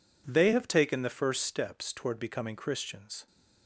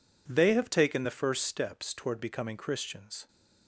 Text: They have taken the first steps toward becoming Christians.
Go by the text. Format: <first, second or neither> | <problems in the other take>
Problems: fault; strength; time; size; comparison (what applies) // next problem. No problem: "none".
neither | none